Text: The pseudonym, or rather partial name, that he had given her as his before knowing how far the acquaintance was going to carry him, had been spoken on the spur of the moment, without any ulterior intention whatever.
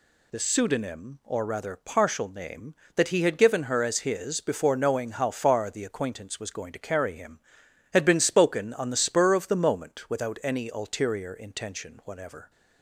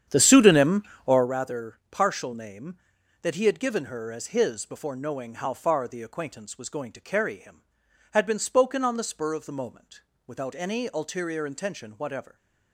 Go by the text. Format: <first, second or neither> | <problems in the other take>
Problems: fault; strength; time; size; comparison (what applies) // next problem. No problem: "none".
first | starts louder than the rest; strong; until 1.3 s; 9 dB